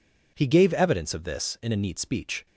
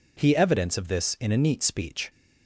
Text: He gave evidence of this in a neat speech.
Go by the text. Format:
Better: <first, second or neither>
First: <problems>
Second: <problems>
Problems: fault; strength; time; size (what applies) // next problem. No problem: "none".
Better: first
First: none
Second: skips "gave"; at 0.3 s